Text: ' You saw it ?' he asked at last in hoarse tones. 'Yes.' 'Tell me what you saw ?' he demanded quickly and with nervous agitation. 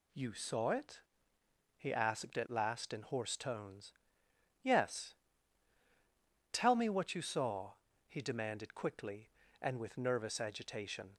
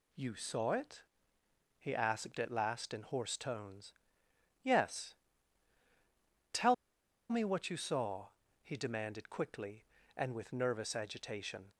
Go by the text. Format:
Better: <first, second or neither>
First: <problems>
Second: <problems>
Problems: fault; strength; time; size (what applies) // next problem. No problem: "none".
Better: first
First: none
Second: pauses between "Tell" and "me"; noticeable; at 6.7 s; 0.55 s long